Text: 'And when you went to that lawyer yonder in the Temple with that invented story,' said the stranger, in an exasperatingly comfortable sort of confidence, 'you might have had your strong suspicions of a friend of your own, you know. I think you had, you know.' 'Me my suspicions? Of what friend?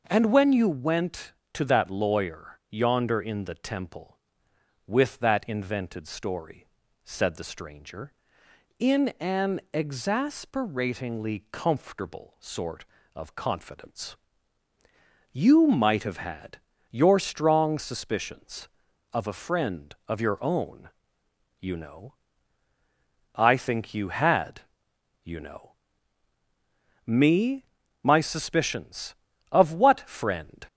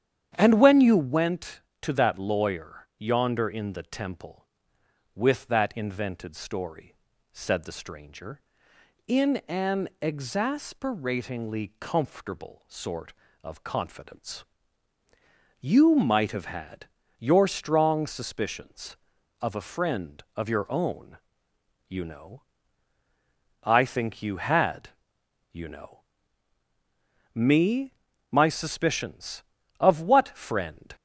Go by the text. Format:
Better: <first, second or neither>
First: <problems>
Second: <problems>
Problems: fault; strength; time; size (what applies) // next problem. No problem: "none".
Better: first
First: pauses between "had" and "your"; slight; at 16.5 s; 0.32 s long // pauses between "Me" and "my"; at 27.6 s; 0.38 s long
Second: starts louder than the rest; strong; until 1.3 s; 9.5 dB // pauses between "had" and "your"; slight; at 16.8 s; 0.32 s long // pauses between "Me" and "my"; at 27.9 s; 0.38 s long